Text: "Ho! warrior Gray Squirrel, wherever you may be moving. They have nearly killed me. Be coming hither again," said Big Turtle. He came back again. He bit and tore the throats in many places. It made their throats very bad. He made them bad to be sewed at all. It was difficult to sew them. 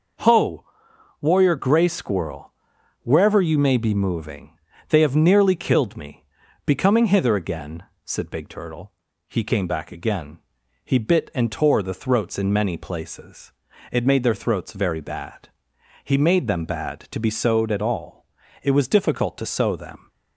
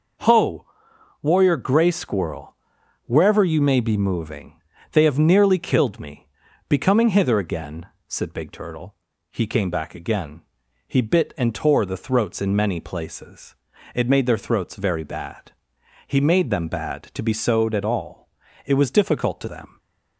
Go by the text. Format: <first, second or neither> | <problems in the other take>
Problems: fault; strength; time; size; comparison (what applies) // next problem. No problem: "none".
first | skips "sew"; at 19.4 s